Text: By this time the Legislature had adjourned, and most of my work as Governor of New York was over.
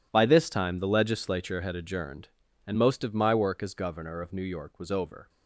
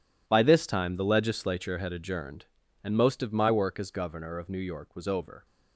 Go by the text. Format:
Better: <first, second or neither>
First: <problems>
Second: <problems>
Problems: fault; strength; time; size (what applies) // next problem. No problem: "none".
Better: neither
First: none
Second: none